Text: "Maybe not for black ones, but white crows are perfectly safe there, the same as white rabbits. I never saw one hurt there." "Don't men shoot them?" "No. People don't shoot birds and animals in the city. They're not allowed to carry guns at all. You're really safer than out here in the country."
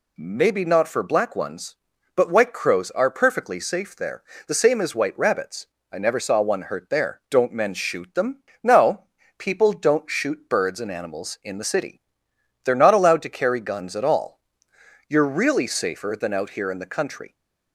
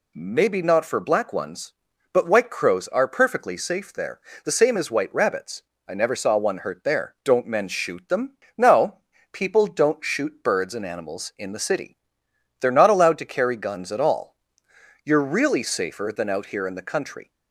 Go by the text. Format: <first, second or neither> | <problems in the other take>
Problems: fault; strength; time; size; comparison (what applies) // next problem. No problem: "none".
neither | none